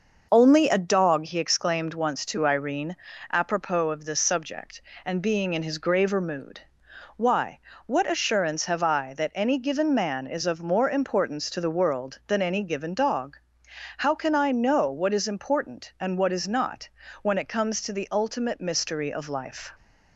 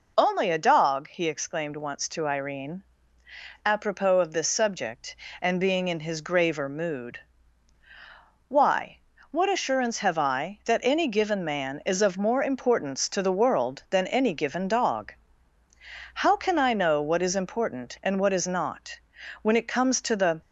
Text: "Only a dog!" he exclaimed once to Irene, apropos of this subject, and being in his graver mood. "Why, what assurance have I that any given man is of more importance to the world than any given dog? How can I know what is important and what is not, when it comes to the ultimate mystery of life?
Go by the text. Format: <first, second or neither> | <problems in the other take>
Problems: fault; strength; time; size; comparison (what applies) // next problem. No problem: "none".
first | stops before "ultimate mystery of life"; at 20.4 s